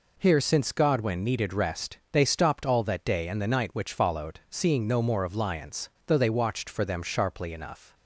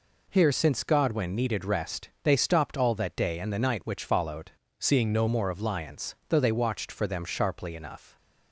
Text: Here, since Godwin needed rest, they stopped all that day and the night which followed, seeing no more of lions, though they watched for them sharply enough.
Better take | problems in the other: first | changes voice from "seeing" to "no"; from 4.7 to 5.2 s; 0.5 s long

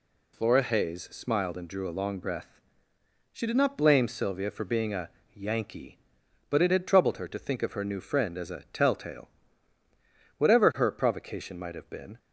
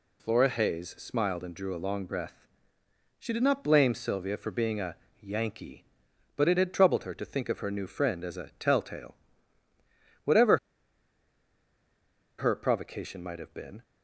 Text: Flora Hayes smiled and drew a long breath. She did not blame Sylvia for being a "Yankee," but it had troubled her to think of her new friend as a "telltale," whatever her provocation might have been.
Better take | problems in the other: first | pauses between "a" and "Yankee"; slight; at 4.9 s; 0.24 s long; slight in the first // pauses between "whatever" and "her"; strong; at 10.5 s; 1.8 s long

